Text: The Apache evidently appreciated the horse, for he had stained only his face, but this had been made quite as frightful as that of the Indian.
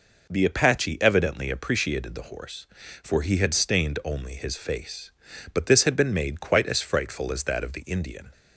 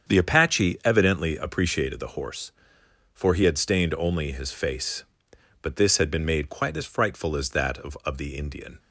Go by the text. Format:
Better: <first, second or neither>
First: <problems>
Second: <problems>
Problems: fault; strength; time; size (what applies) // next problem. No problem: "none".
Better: first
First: none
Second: starts louder than the rest; strong; until 1.1 s; 7.5 dB // says "of" twice; at 8.0 s